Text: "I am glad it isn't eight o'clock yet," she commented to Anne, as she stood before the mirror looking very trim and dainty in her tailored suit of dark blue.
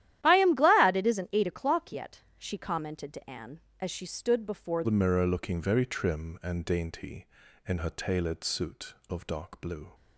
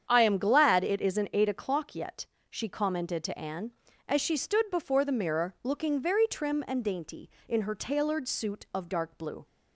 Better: second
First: starts louder than the rest; strong; until 1.2 s; 12.5 dB // changes voice at "the"; from 4.8 s on; 5.1 s long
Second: starts louder than the rest; strong; until 1.1 s; 8 dB

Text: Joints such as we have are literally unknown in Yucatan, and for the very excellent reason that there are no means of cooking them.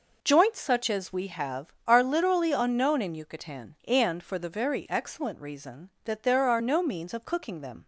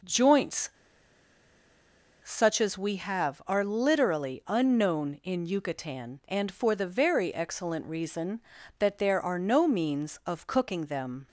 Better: first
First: none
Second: pauses between "Joints" and "such"; strong; at 0.6 s; 1.5 s long

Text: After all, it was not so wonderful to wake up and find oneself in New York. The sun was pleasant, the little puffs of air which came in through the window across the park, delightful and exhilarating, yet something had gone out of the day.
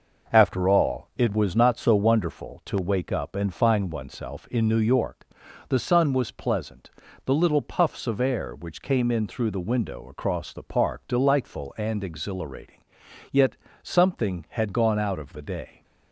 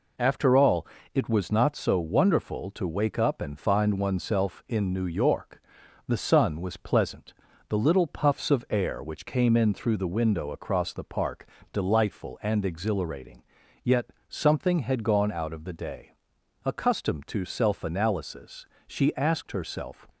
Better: first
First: pauses between "yet" and "something"; slight; at 13.5 s; 0.28 s long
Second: pauses between "yet" and "something"; slight; at 14.1 s; 0.18 s long // goes on to say "Accustomed to self analysis she asked herself"; strong; from 16.6 s on; 3.4 s long

